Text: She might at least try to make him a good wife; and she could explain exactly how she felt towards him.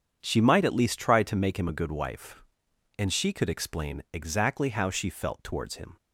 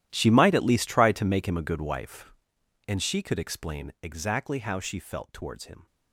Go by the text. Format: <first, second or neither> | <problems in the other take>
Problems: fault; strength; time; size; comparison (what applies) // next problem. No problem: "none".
first | gets quieter; strong; throughout; 19 dB // starts louder than the rest; strong; until 1.1 s; 12.5 dB; strong in the first